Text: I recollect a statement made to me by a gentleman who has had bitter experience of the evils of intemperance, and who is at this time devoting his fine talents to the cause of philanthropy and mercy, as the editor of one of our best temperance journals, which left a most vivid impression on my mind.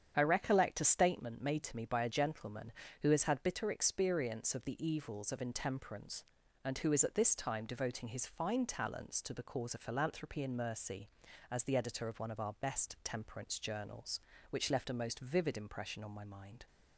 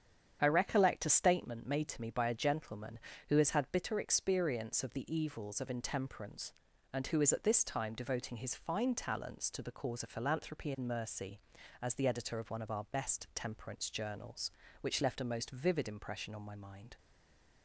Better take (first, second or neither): first